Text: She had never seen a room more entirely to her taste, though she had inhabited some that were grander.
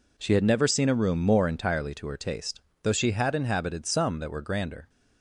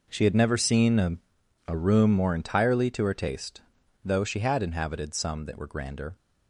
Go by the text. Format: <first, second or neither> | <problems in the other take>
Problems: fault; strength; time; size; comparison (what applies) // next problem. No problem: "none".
first | says "a" twice; at 1.6 s